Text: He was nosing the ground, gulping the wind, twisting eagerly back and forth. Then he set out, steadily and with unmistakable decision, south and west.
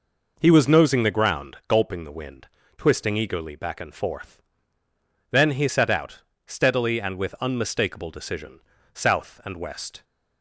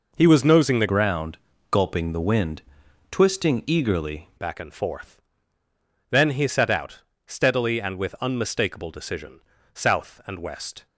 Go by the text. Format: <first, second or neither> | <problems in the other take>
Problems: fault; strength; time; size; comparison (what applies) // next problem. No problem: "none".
first | changes voice from "ground" to "eagerly"; from 0.8 to 4.2 s; 3.4 s long